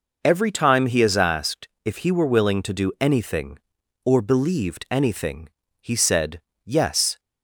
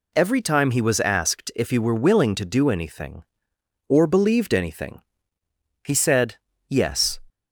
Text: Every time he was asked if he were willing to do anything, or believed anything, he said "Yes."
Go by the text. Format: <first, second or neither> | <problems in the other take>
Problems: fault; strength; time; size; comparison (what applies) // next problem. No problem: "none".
second | says "is" for "was"; at 1.0 s // pauses between "asked" and "if"; slight; at 1.6 s; 0.16 s long // pauses between "said" and "Yes"; slight; at 6.4 s; 0.24 s long; slight in the second